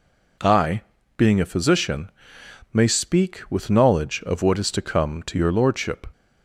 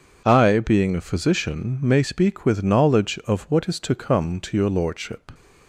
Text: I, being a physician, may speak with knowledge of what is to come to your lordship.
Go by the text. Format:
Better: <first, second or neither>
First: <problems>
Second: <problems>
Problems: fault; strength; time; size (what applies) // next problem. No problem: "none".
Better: neither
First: none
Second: none